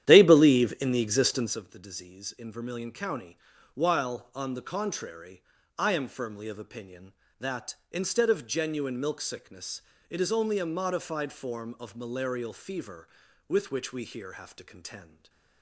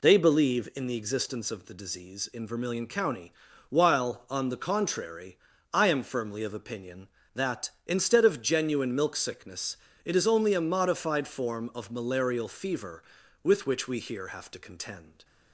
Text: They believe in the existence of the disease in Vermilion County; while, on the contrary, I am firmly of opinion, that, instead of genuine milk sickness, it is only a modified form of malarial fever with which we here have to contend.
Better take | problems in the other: second | starts louder than the rest; strong; until 1.6 s; 11 dB // stays silent after the last word; slight; from 15.0 s on; 0.6 s long

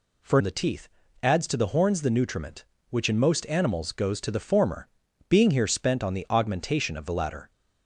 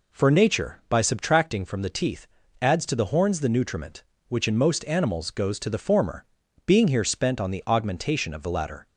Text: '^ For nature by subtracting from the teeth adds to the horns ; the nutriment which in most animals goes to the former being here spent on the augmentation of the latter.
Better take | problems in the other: second | skips "nature by subtracting from"; at 0.4 s // pauses between "teeth" and "adds"; slight; at 0.8 s; 0.34 s long; slight in the second // pauses between "former" and "being"; at 4.8 s; 0.40 s long; also in the second

